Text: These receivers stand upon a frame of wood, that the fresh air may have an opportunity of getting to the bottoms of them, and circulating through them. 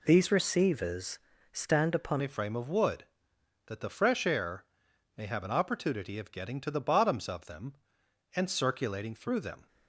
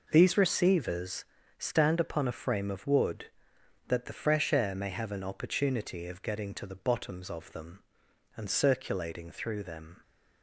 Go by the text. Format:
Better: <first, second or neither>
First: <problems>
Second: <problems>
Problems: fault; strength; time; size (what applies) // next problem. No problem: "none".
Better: second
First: pauses between "receivers" and "stand"; slight; at 1.1 s; 0.34 s long // changes voice at "a"; from 2.2 s on; 7.4 s long // pauses between "air" and "may"; noticeable; at 4.6 s; 0.52 s long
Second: pauses between "receivers" and "stand"; slight; at 1.2 s; 0.34 s long